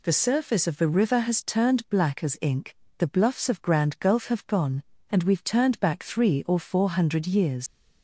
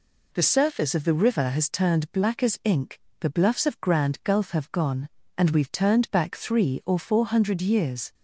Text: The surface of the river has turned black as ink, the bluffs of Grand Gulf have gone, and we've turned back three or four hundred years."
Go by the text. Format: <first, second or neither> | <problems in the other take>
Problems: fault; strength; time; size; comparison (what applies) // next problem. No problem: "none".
second | leaves "years" unfinished; at 7.6 s; 95 ms